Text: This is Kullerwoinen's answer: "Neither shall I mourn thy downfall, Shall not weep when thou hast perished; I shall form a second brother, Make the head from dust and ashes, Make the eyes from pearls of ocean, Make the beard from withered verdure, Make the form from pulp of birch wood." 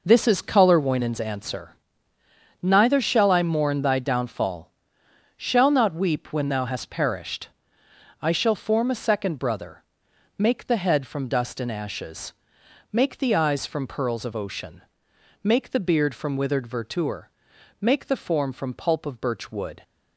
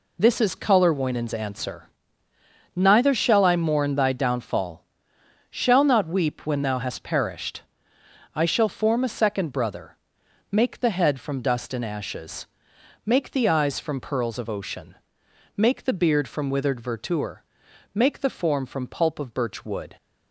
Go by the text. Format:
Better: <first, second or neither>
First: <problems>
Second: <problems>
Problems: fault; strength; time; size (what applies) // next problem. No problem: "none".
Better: second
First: starts louder than the rest; noticeable; until 1.3 s; 5 dB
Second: none